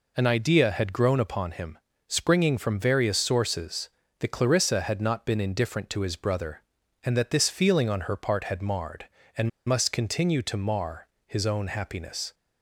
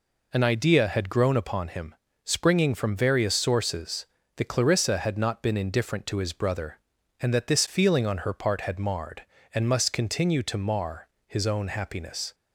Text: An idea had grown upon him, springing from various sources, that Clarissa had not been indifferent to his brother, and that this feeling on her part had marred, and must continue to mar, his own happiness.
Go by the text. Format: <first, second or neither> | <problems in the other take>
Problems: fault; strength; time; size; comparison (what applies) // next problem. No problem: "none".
second | pauses between "and" and "must"; slight; at 9.4 s; 0.17 s long